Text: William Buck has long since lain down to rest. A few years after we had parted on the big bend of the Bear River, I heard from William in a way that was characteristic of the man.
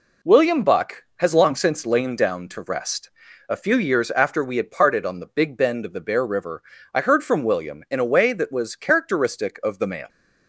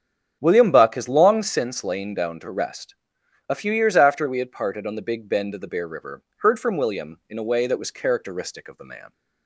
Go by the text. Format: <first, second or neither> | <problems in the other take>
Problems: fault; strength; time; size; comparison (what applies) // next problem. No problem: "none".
first | starts louder than the rest; strong; until 1.4 s; 8 dB // skips "I"; at 6.3 s